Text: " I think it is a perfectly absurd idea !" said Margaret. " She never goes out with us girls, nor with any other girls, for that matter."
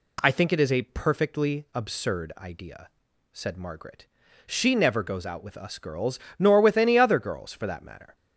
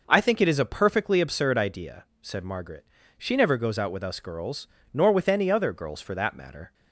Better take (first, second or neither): neither